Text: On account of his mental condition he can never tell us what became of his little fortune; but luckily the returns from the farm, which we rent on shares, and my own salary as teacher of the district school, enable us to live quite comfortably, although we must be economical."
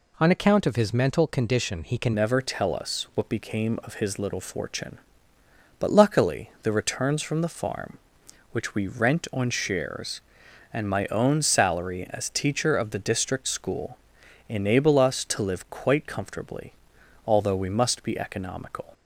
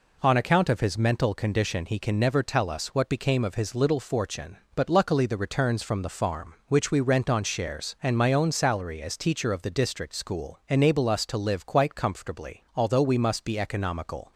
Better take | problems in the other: second | changes voice at "never"; from 2.1 s on; 16.7 s long

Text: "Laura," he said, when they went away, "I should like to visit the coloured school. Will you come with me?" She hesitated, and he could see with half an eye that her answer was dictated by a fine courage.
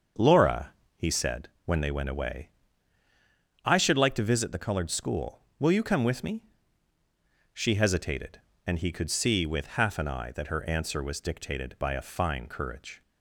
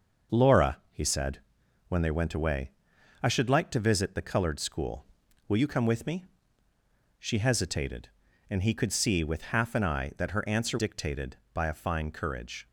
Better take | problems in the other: first | starts louder than the rest; noticeable; until 1.9 s; 6 dB; also in the first // skips "was"; at 10.7 s

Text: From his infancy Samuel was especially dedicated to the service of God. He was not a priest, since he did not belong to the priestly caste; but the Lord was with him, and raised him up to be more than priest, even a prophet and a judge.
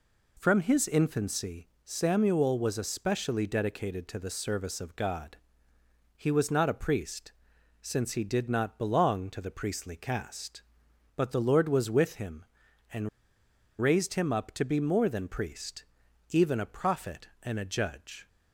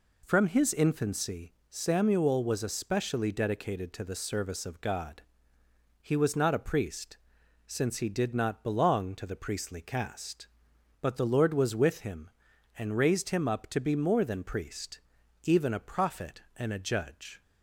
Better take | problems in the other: second | pauses between "infancy" and "Samuel"; slight; at 1.6 s; 0.18 s long; slight in the second // pauses between "and" and "raised"; noticeable; at 13.0 s; 0.72 s long

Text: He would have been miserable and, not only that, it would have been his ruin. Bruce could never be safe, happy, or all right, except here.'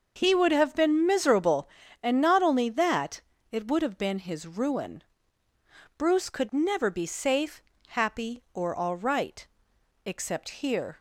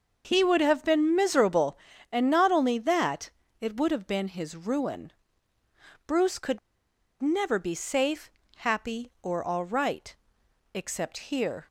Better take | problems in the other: first | starts louder than the rest; until 1.2 s; 6 dB; also in the first // pauses between "could" and "never"; noticeable; at 6.5 s; 0.62 s long

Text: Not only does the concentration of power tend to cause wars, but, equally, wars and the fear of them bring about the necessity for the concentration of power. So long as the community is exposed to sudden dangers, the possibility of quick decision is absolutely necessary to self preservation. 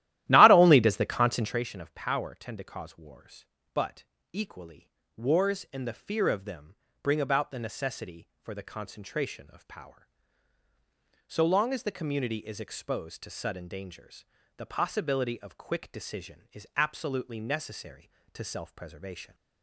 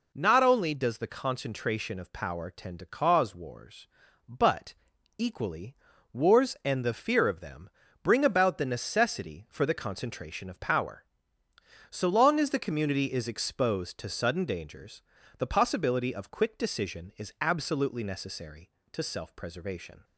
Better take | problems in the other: second | starts louder than the rest; strong; until 1.6 s; 14 dB // pauses between "them" and "bring"; slight; at 6.7 s; 0.28 s long; slight in the second

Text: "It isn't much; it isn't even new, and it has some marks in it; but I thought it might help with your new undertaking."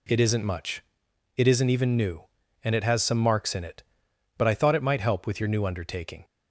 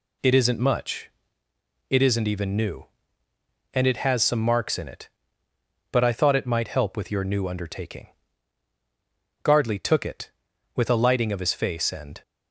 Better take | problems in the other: first | goes on to say "Gardley took it with a lighting of his face and"; strong; from 9.4 s on; 2.7 s long

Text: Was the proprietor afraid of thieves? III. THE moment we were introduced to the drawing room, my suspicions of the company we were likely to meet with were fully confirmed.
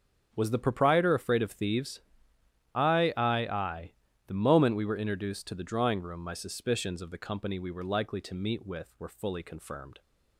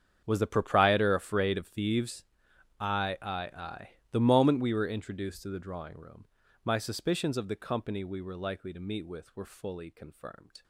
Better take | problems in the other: first | gets quieter; strong; throughout; 18.5 dB // starts louder than the rest; strong; until 1.2 s; 8 dB; strong in the first

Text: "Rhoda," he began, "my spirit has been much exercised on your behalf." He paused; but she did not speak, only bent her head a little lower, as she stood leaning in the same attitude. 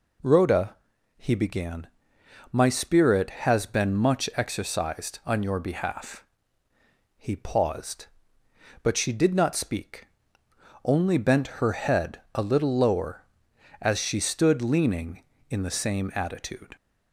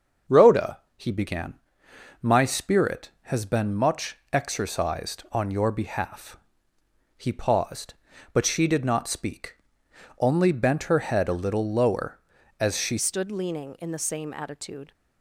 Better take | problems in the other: first | starts louder than the rest; until 1.4 s; 6.5 dB // pauses between "much" and "exercised"; slight; at 4.1 s; 0.16 s long // changes voice at "stood"; from 12.9 s on; 2.0 s long

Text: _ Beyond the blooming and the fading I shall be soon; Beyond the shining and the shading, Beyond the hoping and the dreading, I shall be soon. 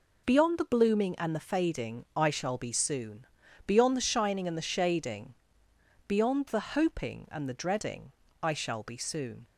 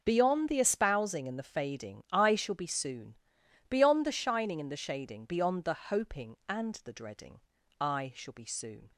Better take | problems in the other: first | says "espousing" for "blooming"; at 0.5 s

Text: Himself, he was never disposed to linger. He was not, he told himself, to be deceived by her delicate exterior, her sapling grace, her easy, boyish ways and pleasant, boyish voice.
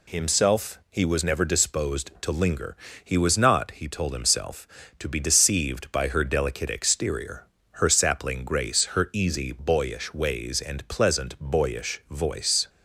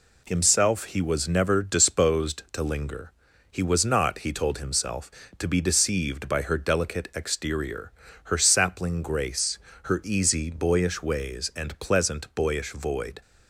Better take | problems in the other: first | says "void" for "voice"; at 12.7 s

